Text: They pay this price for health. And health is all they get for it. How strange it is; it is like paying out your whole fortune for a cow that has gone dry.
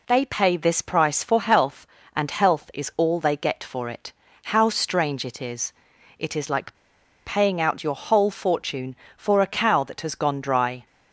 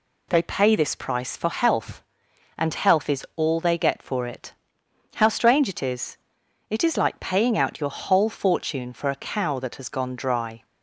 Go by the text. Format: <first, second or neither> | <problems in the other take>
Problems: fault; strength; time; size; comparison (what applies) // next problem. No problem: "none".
second | pauses between "like" and "paying"; noticeable; at 6.7 s; 0.51 s long